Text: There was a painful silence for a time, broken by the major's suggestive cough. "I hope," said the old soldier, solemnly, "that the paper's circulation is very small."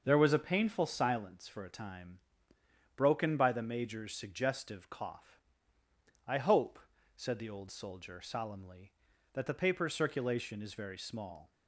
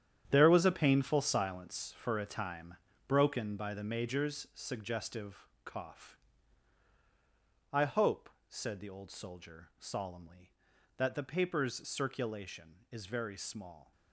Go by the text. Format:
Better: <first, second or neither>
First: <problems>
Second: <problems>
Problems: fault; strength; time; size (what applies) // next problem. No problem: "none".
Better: first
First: none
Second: gets quieter; strong; throughout; 12 dB // pauses between "suggestive" and "cough"; slight; at 5.4 s; 0.18 s long